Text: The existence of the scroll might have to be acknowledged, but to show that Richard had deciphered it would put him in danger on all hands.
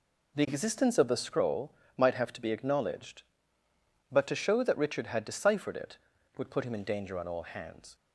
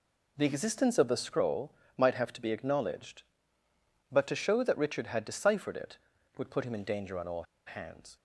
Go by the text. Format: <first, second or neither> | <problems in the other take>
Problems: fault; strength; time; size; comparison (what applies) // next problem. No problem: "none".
first | pauses between "scroll" and "might"; slight; at 1.7 s; 0.26 s long; slight in the first // pauses between "all" and "hands"; slight; at 7.4 s; 0.23 s long